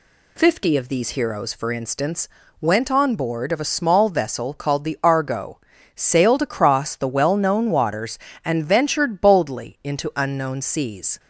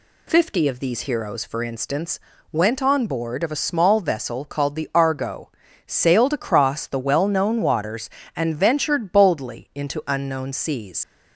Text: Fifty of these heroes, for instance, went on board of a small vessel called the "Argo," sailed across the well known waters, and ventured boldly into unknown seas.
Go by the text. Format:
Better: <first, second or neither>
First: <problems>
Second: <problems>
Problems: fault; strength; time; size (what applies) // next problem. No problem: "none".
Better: first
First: none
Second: leaves "seas" unfinished; at 11.0 s; 70 ms